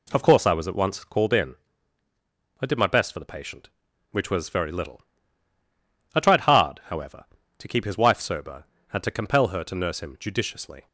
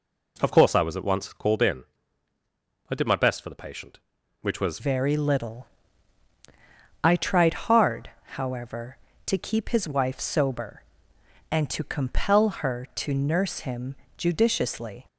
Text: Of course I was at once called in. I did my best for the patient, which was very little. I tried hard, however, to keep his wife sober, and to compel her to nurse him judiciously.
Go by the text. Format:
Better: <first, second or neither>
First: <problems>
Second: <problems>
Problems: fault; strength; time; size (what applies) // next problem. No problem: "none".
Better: first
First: none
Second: changes voice at "very"; from 4.7 s on; 10.3 s long // pauses between "him" and "judiciously"; slight; at 13.9 s; 0.22 s long